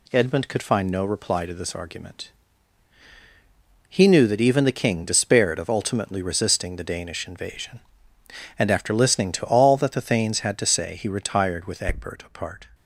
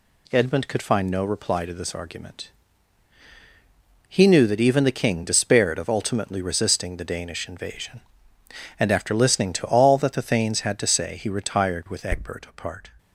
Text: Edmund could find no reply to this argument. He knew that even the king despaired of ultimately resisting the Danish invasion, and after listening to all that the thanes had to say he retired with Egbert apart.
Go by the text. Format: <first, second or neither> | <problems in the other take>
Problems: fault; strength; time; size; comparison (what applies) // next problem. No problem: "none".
neither | none